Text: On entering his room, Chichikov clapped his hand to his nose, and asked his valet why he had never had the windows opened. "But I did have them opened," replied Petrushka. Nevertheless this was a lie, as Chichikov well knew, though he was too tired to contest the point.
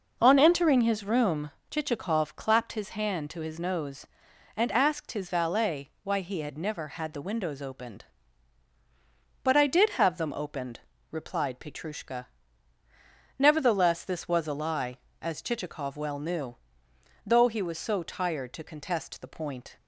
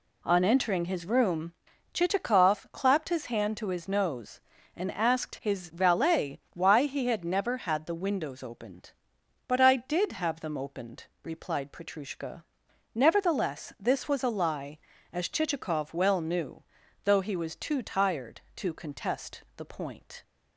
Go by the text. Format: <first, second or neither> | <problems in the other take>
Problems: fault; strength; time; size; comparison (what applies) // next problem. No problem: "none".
second | says "so" for "too"; at 17.7 s